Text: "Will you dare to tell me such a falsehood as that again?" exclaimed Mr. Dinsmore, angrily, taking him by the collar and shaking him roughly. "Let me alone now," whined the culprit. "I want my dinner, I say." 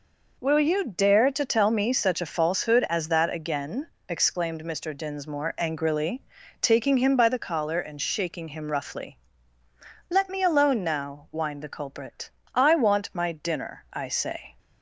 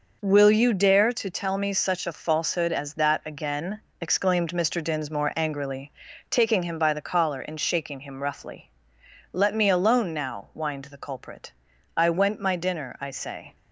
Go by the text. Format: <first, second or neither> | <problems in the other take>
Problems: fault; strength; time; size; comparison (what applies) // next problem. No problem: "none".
first | says "went" for "want"; at 12.0 s